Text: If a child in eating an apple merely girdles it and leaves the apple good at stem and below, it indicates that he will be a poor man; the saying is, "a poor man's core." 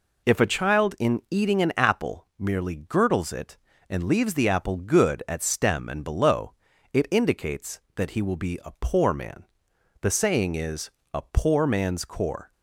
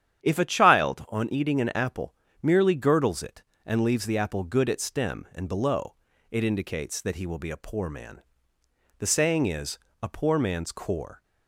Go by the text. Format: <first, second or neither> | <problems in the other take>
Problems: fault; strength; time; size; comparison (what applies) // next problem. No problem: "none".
first | starts louder than the rest; strong; until 1.2 s; 9.5 dB // says "on" for "in"; at 1.0 s // pauses between "apple" and "merely"; slight; at 2.1 s; 0.30 s long